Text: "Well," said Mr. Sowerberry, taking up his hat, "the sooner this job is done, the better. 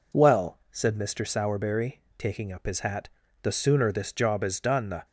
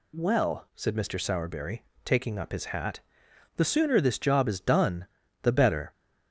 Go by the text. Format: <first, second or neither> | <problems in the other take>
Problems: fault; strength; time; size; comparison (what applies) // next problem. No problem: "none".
second | stops before "better"; at 5.0 s